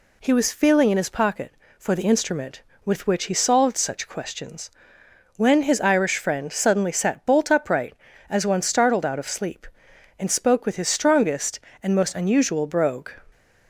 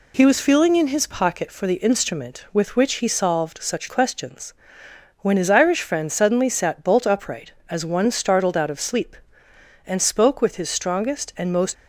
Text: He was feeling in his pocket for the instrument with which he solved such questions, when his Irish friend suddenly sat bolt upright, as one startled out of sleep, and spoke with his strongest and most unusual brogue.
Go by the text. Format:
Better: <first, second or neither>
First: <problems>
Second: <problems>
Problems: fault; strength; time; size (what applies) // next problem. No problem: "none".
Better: first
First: none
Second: stops before "unusual brogue"; at 11.7 s